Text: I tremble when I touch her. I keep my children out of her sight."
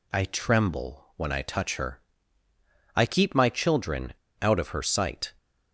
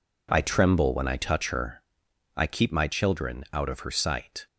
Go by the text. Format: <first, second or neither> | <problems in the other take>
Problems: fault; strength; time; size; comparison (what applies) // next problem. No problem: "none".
second | pauses between "children" and "out"; slight; at 4.1 s; 0.26 s long